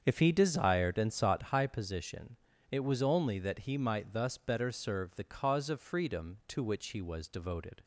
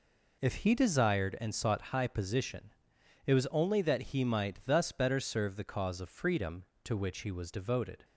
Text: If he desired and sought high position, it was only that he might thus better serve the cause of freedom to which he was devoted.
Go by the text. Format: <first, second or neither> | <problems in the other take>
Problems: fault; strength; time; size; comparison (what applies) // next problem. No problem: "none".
second | starts louder than the rest; strong; until 1.5 s; 7 dB